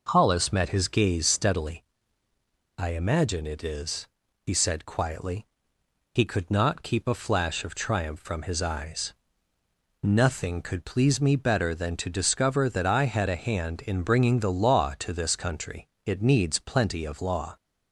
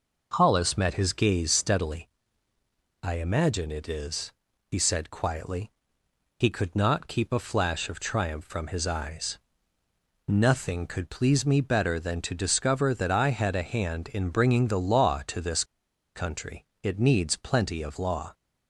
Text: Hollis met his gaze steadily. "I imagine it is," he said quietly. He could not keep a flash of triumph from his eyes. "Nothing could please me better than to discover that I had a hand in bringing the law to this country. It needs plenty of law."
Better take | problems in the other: first | pauses between "this" and "country"; noticeable; at 15.6 s; 0.51 s long

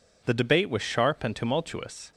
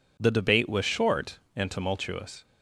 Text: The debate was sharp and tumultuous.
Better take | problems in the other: first | says "short" for "sharp"; at 0.8 s

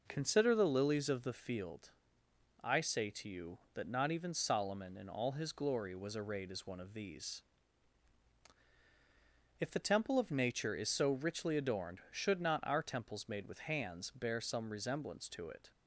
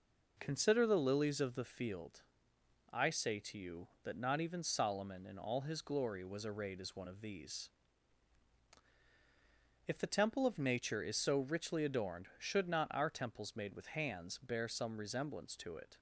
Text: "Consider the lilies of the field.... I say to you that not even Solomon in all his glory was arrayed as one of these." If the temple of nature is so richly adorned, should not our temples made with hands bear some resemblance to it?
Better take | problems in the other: neither | none

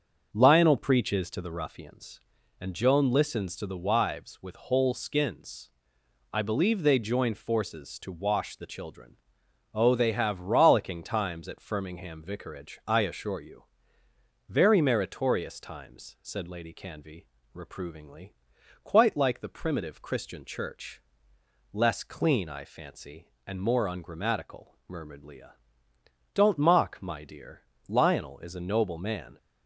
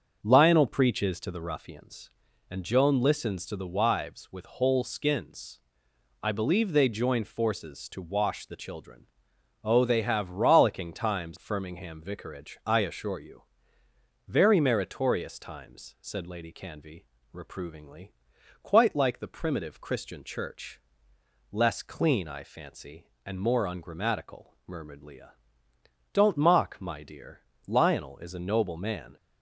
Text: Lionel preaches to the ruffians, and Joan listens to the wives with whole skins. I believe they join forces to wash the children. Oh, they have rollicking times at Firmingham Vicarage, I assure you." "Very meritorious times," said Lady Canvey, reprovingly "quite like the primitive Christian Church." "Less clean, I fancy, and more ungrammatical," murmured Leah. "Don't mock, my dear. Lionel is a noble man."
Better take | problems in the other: first | starts louder than the rest; until 1.2 s; 6.5 dB; also in the first // skips "at"; at 11.3 s // pauses between "reprovingly" and "quite"; noticeable; at 18.0 s; 0.54 s long; noticeable in the first

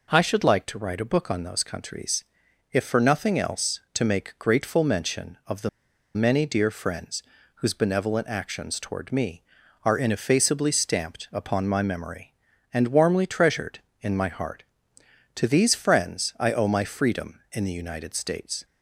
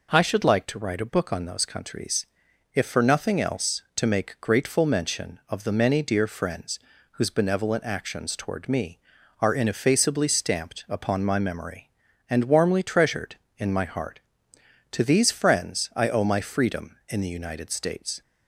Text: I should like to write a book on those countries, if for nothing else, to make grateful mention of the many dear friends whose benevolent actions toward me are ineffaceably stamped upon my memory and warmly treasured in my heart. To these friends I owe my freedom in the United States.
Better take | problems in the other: second | pauses between "the" and "many"; at 5.6 s; 0.45 s long // pauses between "friends" and "whose"; slight; at 7.2 s; 0.32 s long; slight in the second

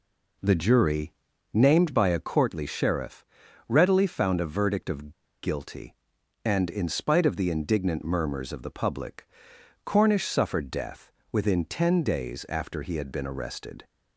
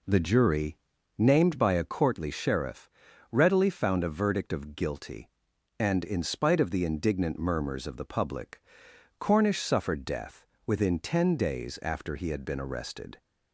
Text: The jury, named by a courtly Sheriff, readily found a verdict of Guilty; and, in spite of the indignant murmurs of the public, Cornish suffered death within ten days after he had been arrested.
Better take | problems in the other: second | pauses between "of" and "Guilty"; slight; at 5.1 s; 0.31 s long // pauses between "death" and "within"; slight; at 11.0 s; 0.22 s long; slight in the second

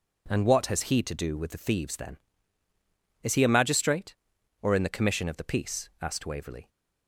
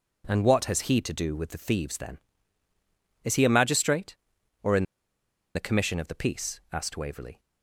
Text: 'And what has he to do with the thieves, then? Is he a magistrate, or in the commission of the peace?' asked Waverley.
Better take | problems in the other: first | pauses between "in" and "the"; noticeable; at 4.8 s; 0.71 s long

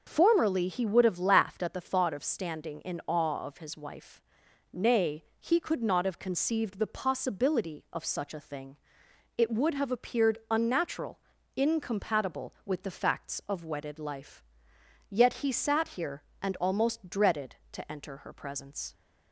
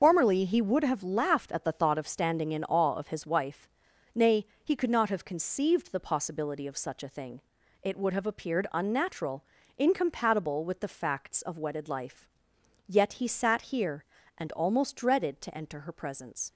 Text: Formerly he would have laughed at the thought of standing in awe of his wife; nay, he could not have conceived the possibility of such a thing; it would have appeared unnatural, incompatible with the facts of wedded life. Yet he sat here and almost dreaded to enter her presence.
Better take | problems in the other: first | loses the start of "Formerly"; at 0.0 s; 45 ms // starts louder than the rest; until 1.0 s; 6 dB

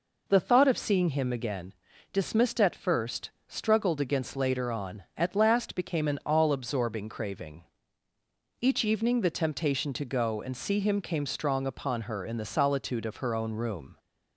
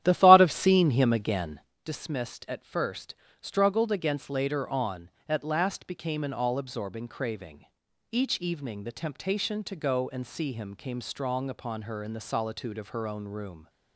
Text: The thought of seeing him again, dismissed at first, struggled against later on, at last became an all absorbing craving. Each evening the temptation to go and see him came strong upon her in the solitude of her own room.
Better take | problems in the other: first | starts louder than the rest; strong; until 1.8 s; 11.5 dB

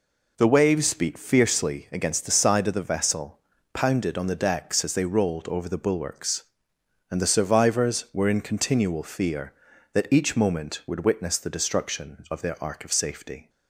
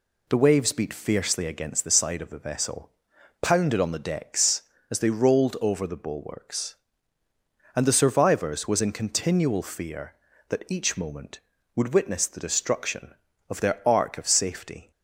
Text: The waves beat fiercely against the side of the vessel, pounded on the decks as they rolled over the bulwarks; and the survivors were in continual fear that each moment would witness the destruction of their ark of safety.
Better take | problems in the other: first | says "was" for "were"; at 8.6 s

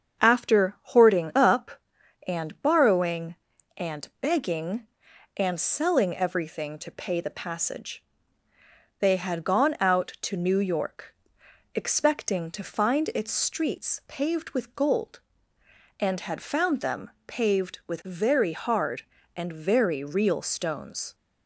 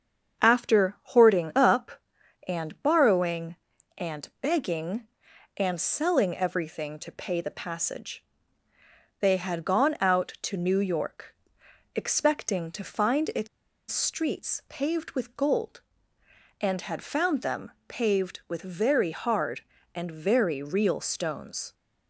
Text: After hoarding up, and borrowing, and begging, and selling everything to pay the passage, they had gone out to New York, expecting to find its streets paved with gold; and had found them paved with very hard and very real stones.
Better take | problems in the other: first | starts louder than the rest; strong; until 1.4 s; 7.5 dB; strong in the first // pauses between "its" and "streets"; at 13.4 s; 0.43 s long // pauses between "them" and "paved"; slight; at 17.7 s; 0.18 s long; slight in the first

